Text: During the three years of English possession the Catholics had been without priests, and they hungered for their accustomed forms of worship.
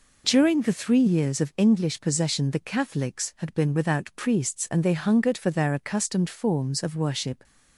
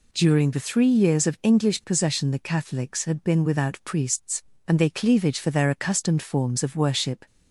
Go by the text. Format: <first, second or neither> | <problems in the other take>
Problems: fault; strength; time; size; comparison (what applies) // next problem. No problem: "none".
first | says "cleavage" for "hungered"; at 4.8 s